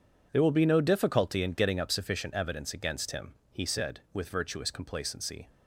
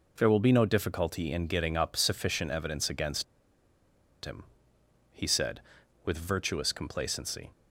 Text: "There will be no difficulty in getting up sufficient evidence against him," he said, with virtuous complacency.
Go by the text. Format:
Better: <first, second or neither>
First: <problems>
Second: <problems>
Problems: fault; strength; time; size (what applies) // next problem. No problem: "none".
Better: first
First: none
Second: pauses between "against" and "him"; at 3.2 s; 1.0 s long